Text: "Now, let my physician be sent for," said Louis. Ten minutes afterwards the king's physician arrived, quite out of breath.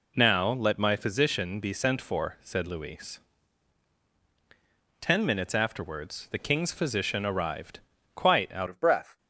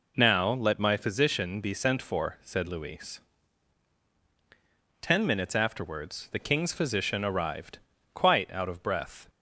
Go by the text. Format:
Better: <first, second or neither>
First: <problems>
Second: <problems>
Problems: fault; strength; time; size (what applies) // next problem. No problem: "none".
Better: second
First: changes voice at "of"; from 8.6 s on; 0.5 s long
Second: none